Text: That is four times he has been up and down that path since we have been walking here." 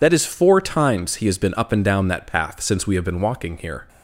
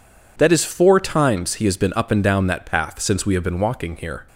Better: second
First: loses the start of "That"; at 0.0 s; 35 ms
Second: none

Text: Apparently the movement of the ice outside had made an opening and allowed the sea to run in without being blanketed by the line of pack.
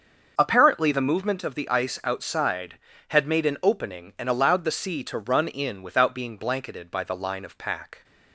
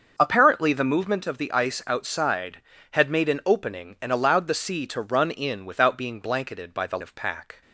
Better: first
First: starts louder than the rest; until 1.3 s; 6.5 dB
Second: starts louder than the rest; until 1.1 s; 6.5 dB // skips "line"; at 6.9 s

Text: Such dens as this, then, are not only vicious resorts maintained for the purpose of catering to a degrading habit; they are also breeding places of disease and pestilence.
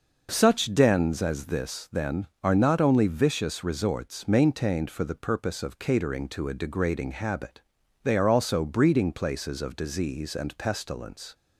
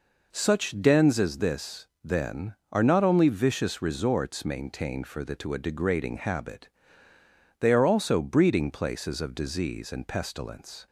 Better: first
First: none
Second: skips "purpose of catering"; at 5.3 s

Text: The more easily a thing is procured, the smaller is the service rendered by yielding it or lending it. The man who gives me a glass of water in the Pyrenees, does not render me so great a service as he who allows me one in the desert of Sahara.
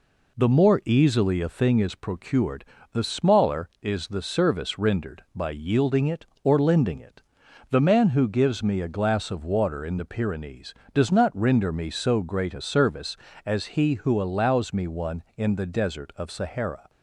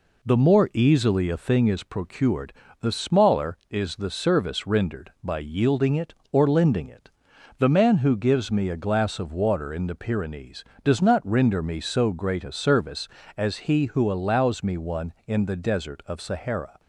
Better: neither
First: none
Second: none

